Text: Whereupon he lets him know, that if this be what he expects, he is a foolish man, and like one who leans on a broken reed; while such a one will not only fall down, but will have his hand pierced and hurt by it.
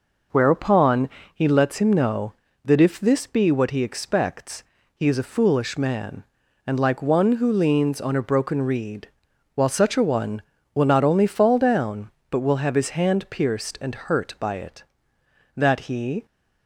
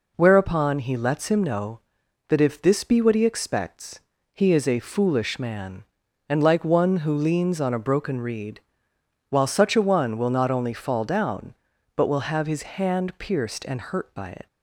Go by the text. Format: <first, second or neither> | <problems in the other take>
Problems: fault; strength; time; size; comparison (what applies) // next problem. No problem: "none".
second | pauses between "Whereupon" and "he"; slight; at 1.0 s; 0.24 s long // goes on to say "That he"; noticeable; from 15.5 s on; 0.70 s long